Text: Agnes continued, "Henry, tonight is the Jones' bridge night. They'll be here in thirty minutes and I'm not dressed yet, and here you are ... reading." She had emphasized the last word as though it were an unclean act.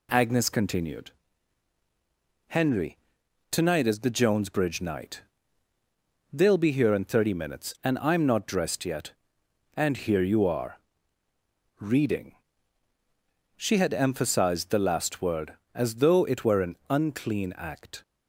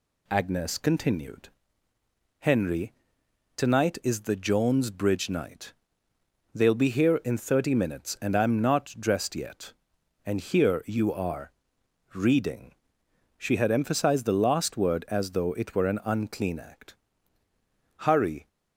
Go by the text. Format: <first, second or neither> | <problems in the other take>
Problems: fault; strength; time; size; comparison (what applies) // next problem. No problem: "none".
first | goes on to say "Hurry"; from 17.9 s on; 0.50 s long